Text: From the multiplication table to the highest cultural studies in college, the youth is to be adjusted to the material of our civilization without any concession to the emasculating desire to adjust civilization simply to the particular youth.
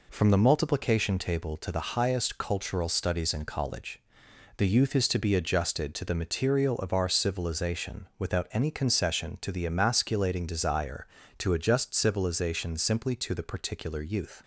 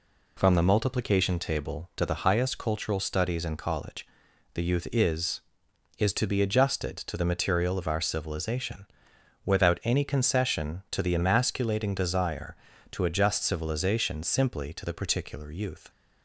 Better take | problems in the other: first | says "is" twice; at 5.9 s // pauses between "civilization" and "without"; noticeable; at 8.8 s; 0.58 s long

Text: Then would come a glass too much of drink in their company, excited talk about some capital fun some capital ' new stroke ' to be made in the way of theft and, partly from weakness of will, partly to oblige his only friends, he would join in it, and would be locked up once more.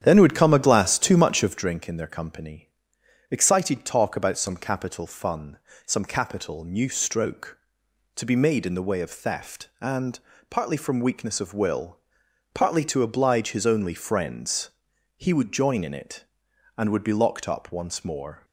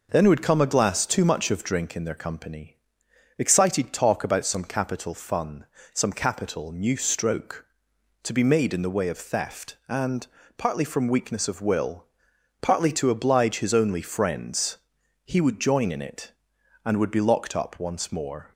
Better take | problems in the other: second | starts louder than the rest; strong; until 1.6 s; 9.5 dB // pauses between "fun" and "some"; slight; at 5.5 s; 0.28 s long; slight in the second

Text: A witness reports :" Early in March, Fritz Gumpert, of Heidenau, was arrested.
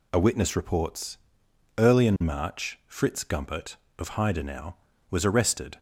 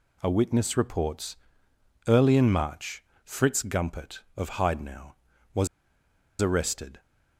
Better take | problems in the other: first | pauses between "was" and "arrested"; noticeable; at 5.6 s; 0.74 s long

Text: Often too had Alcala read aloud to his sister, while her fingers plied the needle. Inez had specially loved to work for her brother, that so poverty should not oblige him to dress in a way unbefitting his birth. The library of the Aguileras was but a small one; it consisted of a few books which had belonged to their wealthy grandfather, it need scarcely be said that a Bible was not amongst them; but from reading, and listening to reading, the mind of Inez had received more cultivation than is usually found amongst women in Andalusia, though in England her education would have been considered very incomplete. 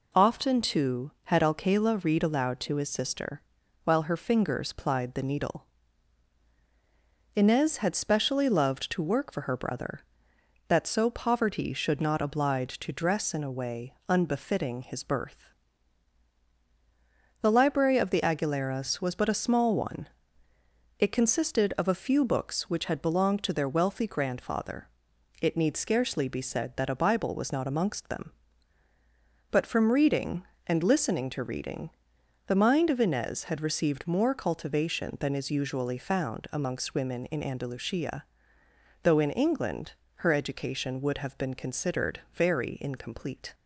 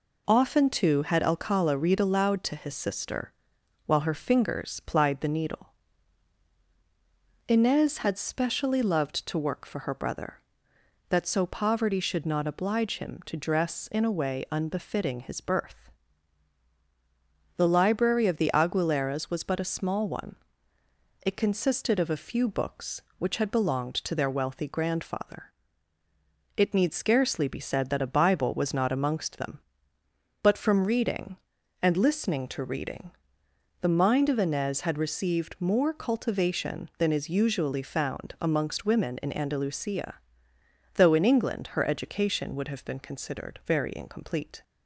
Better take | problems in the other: second | skips "him"; at 12.7 s // pauses between "England" and "her"; slight; at 39.9 s; 0.22 s long

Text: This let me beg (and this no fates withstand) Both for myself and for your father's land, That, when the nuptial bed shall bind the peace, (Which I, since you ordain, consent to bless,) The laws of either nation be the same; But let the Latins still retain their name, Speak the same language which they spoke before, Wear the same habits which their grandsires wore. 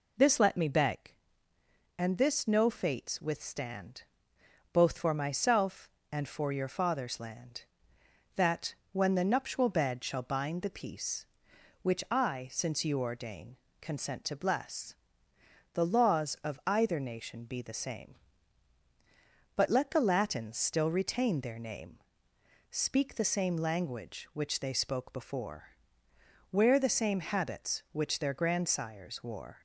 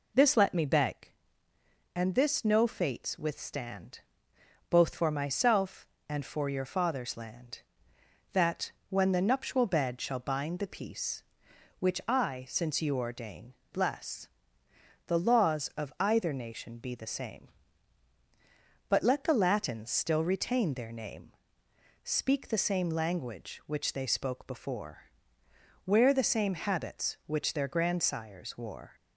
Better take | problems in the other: first | skips "consent to"; at 13.6 s

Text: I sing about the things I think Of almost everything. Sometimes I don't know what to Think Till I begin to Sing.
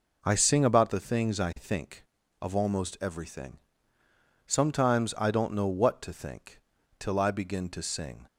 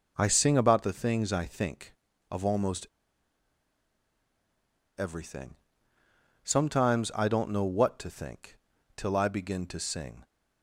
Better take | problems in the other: first | pauses between "almost" and "everything"; strong; at 2.8 s; 2.1 s long // pauses between "Think" and "Till"; at 8.5 s; 0.38 s long; also in the first

